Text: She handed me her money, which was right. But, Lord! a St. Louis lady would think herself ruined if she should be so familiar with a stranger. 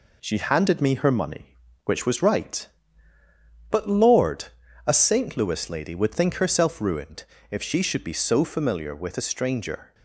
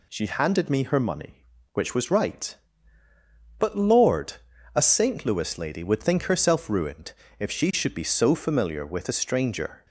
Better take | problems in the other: second | gets quieter; slight; throughout; 3 dB // pauses between "ruined" and "if"; slight; at 7.2 s; 0.26 s long; slight in the second

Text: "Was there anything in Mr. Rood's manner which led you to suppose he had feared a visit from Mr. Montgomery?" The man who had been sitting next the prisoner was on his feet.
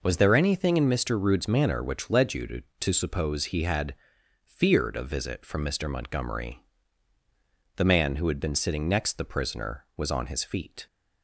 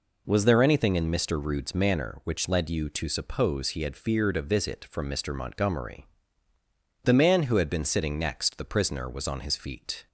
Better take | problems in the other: second | says "to" twice; at 2.8 s // pauses between "had" and "feared"; noticeable; at 3.9 s; 0.52 s long

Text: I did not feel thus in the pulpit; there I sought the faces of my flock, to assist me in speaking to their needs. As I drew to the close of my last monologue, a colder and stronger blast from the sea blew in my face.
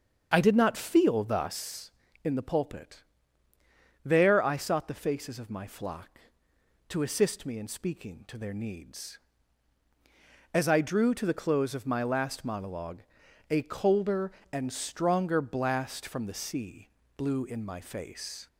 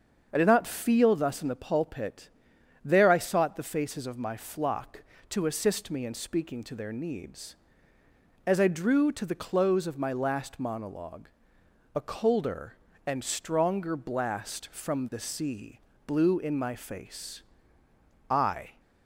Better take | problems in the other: first | starts louder than the rest; until 1.3 s; 7 dB; also in the first // pauses between "sea" and "blew"; slight; at 15.7 s; 0.26 s long; slight in the first // goes on to say "I"; from 18.2 s on; 0.50 s long

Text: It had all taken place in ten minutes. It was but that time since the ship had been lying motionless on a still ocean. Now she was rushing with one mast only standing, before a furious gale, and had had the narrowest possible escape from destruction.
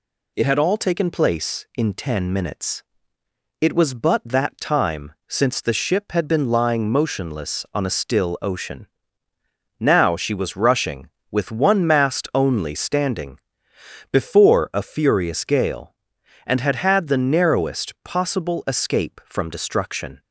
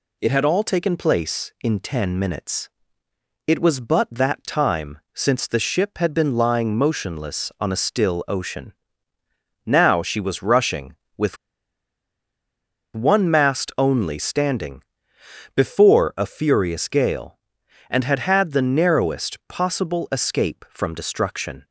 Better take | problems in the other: first | pauses between "with" and "one"; strong; at 11.3 s; 1.5 s long

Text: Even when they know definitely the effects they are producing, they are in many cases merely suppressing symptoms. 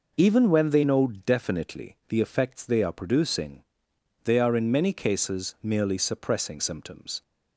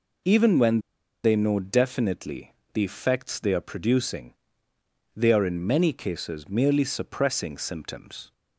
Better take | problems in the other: first | pauses between "when" and "they"; at 0.8 s; 0.42 s long // pauses between "definitely" and "the"; slight; at 2.5 s; 0.20 s long

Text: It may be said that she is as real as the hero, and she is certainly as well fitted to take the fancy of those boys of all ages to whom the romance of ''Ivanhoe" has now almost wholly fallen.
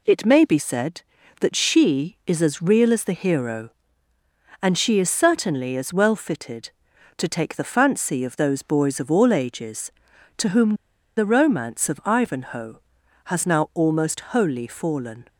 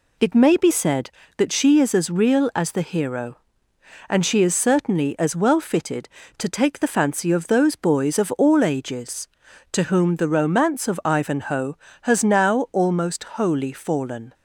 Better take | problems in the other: second | pauses between "whom" and "the"; at 10.7 s; 0.43 s long

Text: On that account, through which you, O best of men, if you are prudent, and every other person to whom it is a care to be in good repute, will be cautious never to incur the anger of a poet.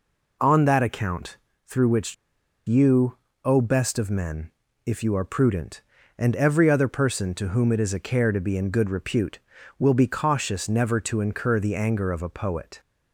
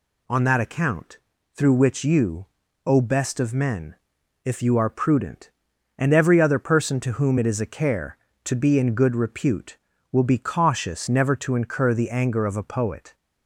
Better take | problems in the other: second | pauses between "which" and "you"; noticeable; at 2.1 s; 0.52 s long

